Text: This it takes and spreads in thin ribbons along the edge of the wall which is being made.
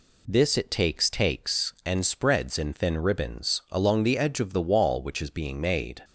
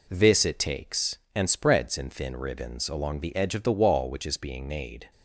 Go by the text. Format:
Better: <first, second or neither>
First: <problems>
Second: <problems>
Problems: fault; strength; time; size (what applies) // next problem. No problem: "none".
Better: second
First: says "takes" twice; at 1.0 s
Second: none